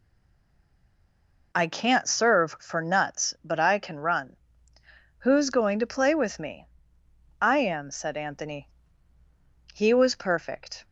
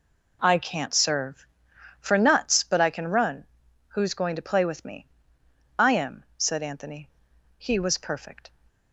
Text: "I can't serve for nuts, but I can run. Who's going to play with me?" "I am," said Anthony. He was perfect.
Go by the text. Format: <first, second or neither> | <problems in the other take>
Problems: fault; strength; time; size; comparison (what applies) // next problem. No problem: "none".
second | stays silent before the first word; noticeable; until 1.5 s; 1.5 s long